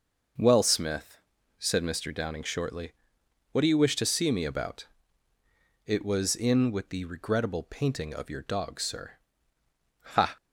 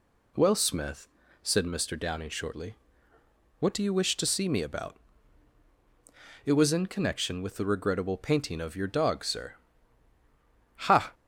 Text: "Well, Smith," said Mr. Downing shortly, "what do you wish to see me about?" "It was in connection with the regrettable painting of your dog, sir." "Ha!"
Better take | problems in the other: second | starts louder than the rest; noticeable; until 1.8 s; 6 dB // skips "connection"; at 6.7 s

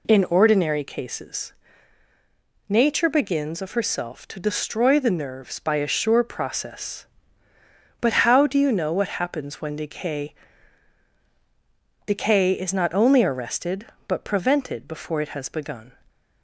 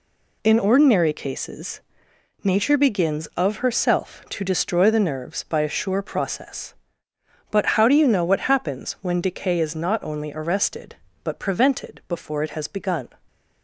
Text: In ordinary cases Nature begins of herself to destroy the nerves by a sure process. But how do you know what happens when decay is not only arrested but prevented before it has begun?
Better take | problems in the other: second | pauses between "cases" and "Nature"; at 1.5 s; 1.1 s long; noticeable in the second // says "decay" twice; at 12.0 s

